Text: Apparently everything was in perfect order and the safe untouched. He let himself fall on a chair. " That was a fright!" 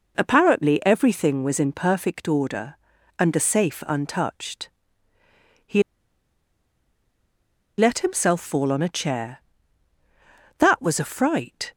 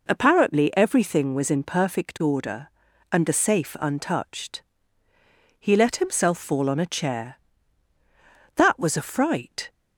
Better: second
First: pauses between "He" and "let"; strong; at 5.8 s; 1.9 s long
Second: none

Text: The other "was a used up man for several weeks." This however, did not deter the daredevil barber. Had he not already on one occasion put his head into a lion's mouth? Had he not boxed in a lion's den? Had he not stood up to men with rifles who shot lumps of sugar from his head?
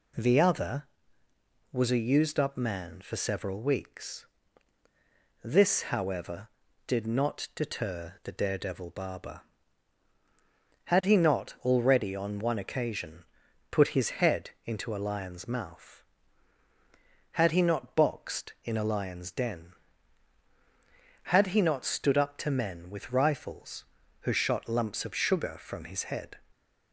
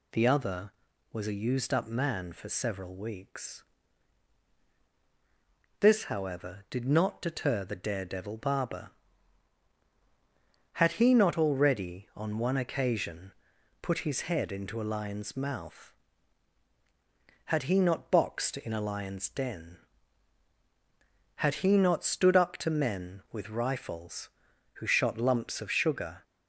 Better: first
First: pauses between "occasion" and "put"; at 13.2 s; 0.44 s long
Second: pauses between "occasion" and "put"; noticeable; at 13.3 s; 0.50 s long // stops before "from his head"; at 26.2 s

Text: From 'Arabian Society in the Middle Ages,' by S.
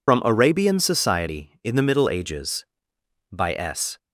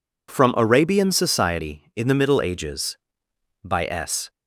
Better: second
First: loses the start of "From"; at 0.0 s; 115 ms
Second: none

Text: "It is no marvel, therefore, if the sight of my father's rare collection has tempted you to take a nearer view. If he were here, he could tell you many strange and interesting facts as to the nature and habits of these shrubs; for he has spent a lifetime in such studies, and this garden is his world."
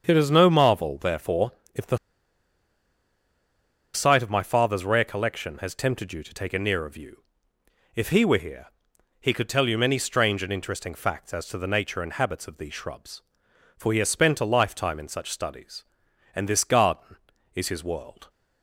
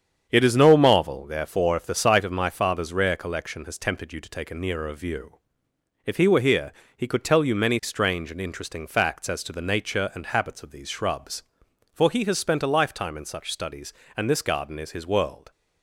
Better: second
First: starts louder than the rest; strong; until 1.0 s; 7 dB // pauses between "the" and "sight"; strong; at 1.9 s; 1.9 s long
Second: starts louder than the rest; strong; until 1.3 s; 8 dB

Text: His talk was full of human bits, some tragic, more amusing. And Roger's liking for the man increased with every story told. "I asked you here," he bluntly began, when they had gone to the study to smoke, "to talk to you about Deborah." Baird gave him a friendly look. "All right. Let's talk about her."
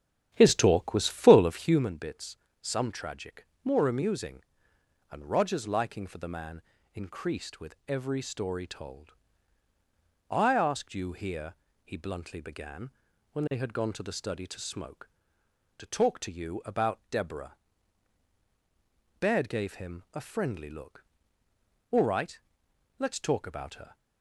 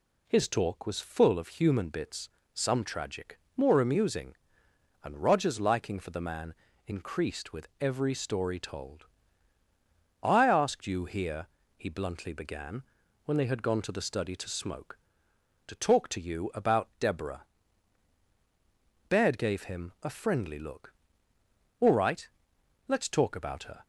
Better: second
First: starts louder than the rest; strong; until 1.8 s; 9.5 dB // pauses between "man" and "increased"; slight; at 6.6 s; 0.34 s long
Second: pauses between "man" and "increased"; slight; at 6.5 s; 0.34 s long

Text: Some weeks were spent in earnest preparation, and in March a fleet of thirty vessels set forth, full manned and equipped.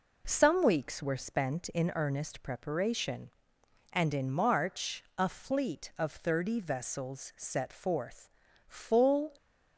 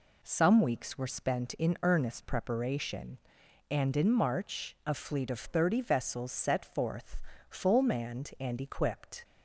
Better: second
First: stops before "manned and equipped"; at 9.3 s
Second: none

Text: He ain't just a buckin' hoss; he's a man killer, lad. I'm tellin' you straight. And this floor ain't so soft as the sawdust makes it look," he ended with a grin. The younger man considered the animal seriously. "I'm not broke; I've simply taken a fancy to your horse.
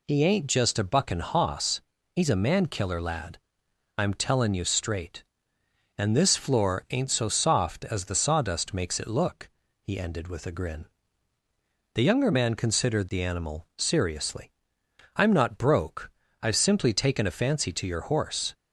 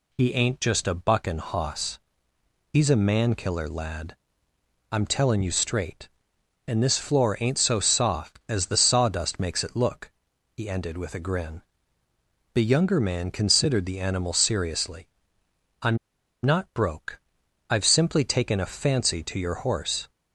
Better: first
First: none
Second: pauses between "I'm" and "not"; at 15.9 s; 0.45 s long

